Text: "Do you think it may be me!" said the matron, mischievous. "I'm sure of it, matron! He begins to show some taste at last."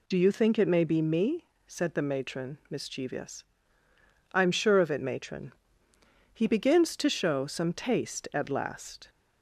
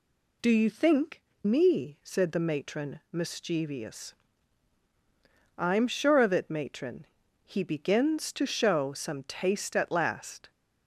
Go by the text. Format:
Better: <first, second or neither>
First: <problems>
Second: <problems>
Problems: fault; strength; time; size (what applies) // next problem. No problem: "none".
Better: first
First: none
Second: skips "it may be"; at 1.3 s